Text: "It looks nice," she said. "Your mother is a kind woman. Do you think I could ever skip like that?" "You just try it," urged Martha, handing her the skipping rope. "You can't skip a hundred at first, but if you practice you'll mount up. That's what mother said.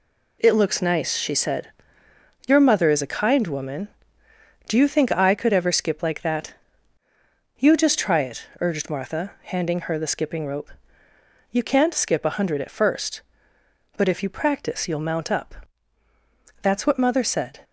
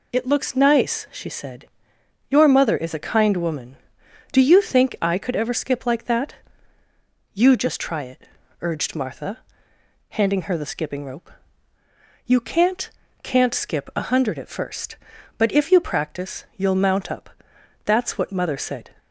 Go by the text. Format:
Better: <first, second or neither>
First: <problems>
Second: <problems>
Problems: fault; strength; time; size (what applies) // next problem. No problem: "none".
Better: first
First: none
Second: says "can't" twice; at 13.2 s